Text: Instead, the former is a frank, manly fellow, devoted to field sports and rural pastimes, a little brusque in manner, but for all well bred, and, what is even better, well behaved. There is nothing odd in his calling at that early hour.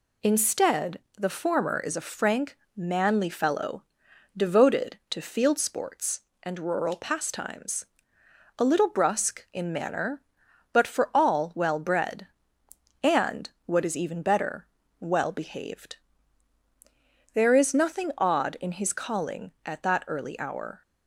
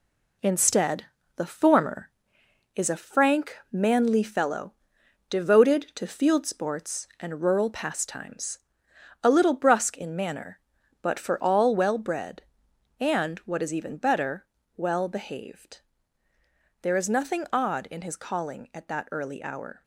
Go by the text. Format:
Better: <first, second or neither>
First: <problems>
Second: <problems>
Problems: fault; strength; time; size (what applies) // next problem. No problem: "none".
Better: first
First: none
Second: gets quieter; throughout; 6.5 dB